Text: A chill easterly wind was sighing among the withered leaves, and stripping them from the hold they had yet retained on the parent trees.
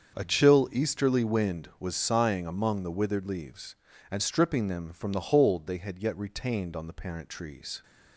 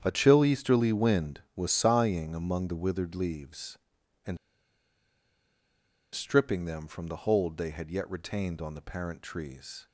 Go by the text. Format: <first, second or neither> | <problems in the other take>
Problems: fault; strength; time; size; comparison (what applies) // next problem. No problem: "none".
first | starts louder than the rest; strong; until 1.0 s; 8.5 dB; also in the first // pauses between "and" and "stripping"; strong; at 4.3 s; 1.7 s long